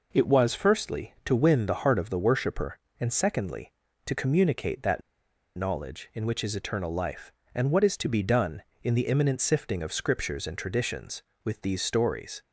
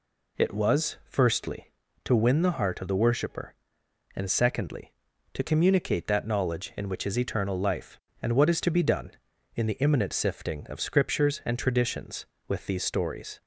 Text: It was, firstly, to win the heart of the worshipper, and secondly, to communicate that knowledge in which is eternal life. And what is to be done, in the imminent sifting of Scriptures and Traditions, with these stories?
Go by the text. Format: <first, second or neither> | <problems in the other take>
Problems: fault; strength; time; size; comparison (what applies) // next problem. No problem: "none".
second | pauses between "that" and "knowledge"; noticeable; at 5.0 s; 0.56 s long